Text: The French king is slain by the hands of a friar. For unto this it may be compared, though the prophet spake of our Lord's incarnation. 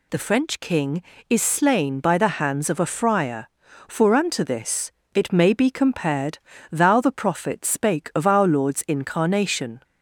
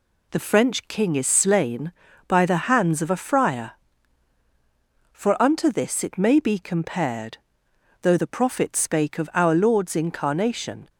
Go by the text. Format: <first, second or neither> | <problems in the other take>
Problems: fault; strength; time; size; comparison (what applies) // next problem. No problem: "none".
second | pauses between "this" and "it"; slight; at 4.9 s; 0.22 s long // says "thou" for "though"; at 6.6 s